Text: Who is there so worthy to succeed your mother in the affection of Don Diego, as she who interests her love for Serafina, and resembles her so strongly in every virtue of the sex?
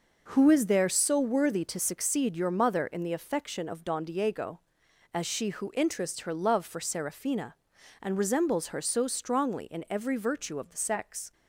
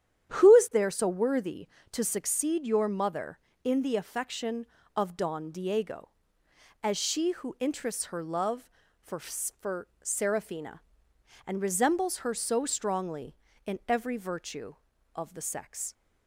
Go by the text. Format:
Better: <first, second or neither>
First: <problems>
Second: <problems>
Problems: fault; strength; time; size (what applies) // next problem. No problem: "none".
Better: first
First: none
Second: starts louder than the rest; strong; until 1.3 s; 9.5 dB // says "for" twice; at 9.1 s